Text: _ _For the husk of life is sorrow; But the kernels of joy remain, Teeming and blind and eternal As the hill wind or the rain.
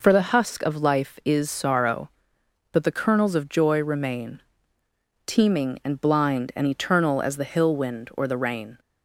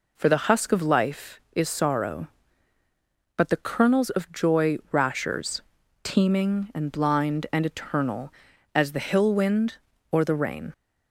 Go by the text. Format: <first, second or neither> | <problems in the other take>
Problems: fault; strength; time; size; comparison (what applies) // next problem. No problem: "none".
first | says "rashers" for "remain"; at 4.9 s